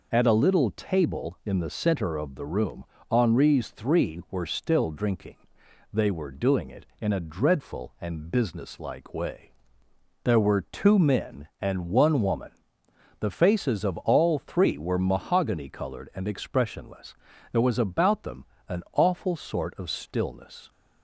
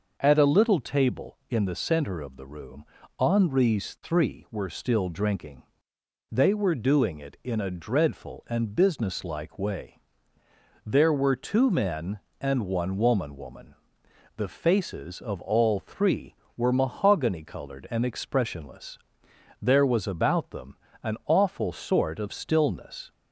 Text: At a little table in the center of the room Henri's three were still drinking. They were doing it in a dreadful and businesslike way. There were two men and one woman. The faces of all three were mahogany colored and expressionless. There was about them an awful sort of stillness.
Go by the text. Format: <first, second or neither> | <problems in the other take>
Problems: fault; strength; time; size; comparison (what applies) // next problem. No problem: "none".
first | pauses between "room" and "Henri's"; slight; at 2.8 s; 0.34 s long; slight in the first // says "woman" twice; at 13.3 s // pauses between "them" and "an"; slight; at 20.7 s; 0.26 s long; slight in the first